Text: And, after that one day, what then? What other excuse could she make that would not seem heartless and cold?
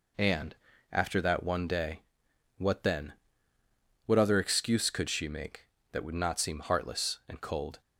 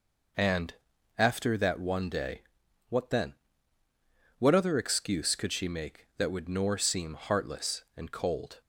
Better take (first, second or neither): first